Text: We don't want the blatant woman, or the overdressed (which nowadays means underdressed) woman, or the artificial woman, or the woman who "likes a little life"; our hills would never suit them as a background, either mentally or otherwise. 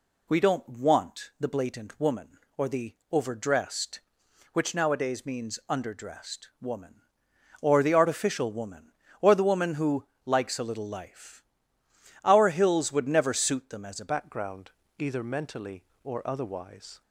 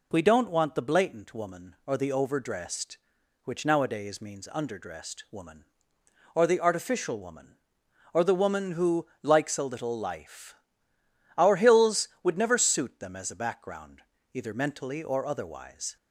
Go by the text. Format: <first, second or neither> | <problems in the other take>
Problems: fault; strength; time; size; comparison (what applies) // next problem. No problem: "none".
second | pauses between "the" and "overdressed"; slight; at 2.9 s; 0.16 s long // pauses between "who" and "likes"; slight; at 10.0 s; 0.20 s long; slight in the second // changes voice at "background"; from 14.0 s on; 3.0 s long